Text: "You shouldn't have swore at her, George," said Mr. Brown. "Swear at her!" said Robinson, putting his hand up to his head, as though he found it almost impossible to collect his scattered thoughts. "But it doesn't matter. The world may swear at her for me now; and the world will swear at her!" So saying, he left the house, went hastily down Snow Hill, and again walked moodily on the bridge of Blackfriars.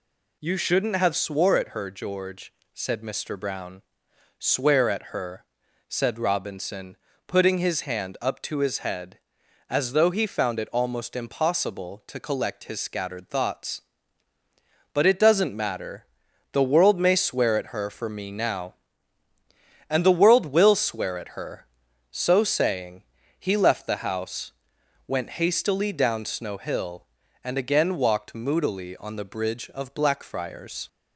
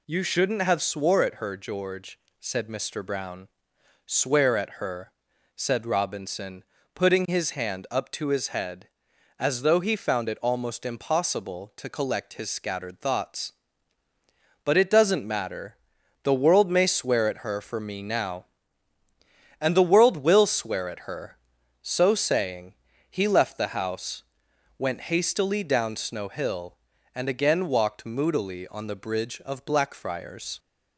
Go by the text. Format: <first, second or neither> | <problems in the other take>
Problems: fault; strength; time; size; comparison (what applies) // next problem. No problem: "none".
neither | none